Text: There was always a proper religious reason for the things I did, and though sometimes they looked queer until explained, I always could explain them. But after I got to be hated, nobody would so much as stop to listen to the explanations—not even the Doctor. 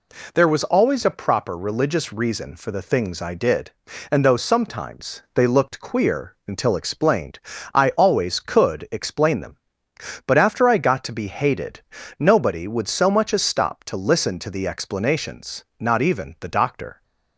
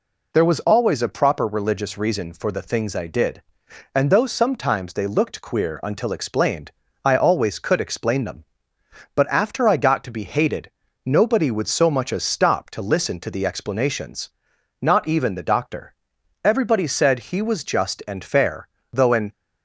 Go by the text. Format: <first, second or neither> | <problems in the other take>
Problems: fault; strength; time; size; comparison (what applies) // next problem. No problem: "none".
first | goes on to say "Everybody said he was just and fair though an"; strong; from 16.4 s on; 2.8 s long